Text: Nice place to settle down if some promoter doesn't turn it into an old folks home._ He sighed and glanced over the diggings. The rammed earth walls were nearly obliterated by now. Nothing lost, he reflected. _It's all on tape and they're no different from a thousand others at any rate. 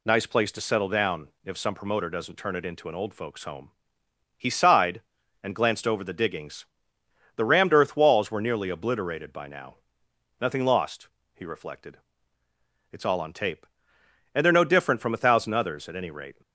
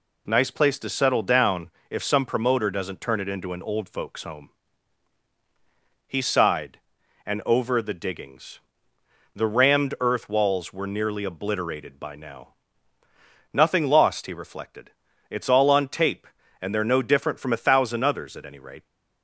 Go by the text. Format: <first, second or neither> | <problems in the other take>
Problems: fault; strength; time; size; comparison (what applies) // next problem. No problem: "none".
first | pauses between "down" and "if"; slight; at 1.7 s; 0.18 s long; slight in the first // skips "glanced"; at 7.4 s